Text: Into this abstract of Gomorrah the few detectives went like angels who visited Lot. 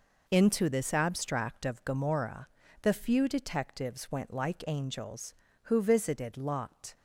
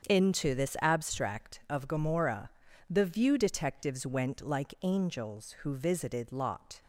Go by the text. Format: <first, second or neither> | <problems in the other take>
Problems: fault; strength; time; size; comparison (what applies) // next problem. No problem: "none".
first | starts louder than the rest; strong; until 1.1 s; 7.5 dB // pauses between "Gomorrah" and "the"; at 2.5 s; 0.38 s long; slight in the first // says "view" for "few"; at 3.0 s